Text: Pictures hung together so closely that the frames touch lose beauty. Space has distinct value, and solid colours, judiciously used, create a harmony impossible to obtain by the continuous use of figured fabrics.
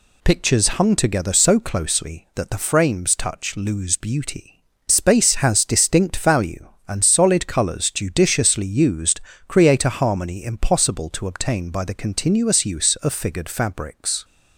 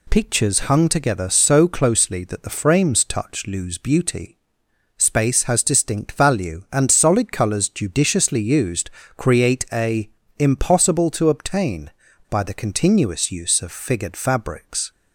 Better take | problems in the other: first | skips "harmony"; at 10.2 s

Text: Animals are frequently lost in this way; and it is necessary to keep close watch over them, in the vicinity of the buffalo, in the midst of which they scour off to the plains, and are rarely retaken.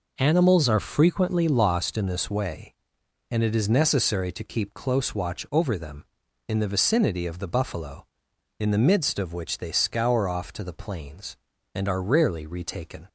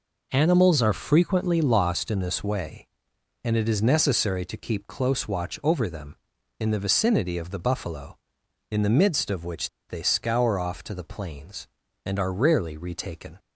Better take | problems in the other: first | pauses between "which" and "they"; slight; at 9.6 s; 0.19 s long

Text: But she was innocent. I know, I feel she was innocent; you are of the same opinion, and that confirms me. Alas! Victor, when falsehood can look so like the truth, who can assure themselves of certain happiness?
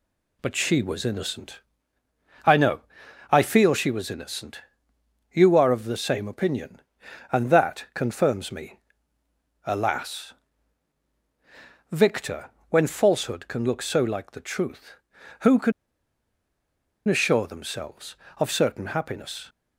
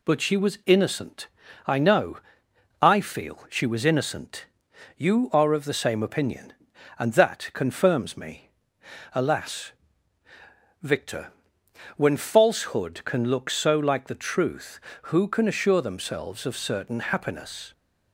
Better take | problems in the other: second | pauses between "can" and "assure"; strong; at 15.7 s; 1.3 s long

